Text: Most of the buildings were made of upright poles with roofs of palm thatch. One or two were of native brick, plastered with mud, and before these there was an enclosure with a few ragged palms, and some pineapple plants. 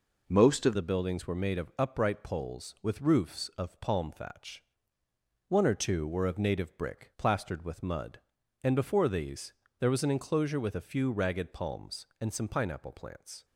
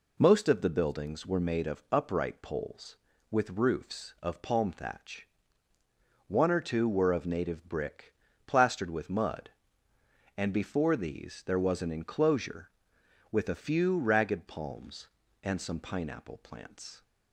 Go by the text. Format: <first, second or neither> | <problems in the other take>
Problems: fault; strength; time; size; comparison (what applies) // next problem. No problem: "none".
second | changes voice at "the"; from 0.7 s on; 12.7 s long // pauses between "these" and "there"; slight; at 9.5 s; 0.26 s long